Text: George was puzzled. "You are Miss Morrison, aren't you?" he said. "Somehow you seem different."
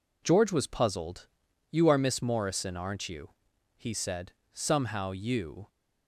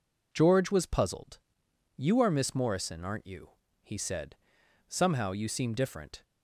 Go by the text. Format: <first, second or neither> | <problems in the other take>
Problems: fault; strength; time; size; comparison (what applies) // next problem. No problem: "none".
second | stops before "seem different"; at 5.6 s